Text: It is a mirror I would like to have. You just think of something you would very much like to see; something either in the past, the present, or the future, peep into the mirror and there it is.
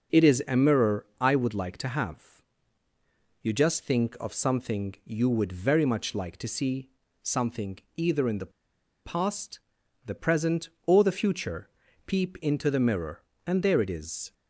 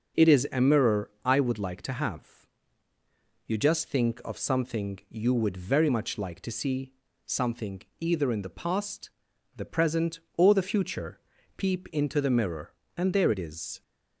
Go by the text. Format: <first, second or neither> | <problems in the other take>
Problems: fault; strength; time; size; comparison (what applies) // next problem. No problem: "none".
second | pauses between "something" and "either"; slight; at 7.7 s; 0.18 s long; slight in the second // pauses between "the" and "past"; noticeable; at 8.5 s; 0.53 s long